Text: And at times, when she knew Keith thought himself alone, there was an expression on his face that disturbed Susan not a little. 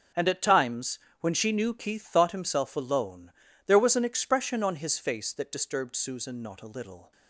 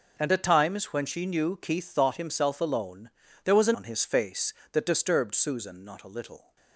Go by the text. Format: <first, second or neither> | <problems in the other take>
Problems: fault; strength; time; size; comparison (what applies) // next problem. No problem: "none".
first | skips "expression"; at 3.7 s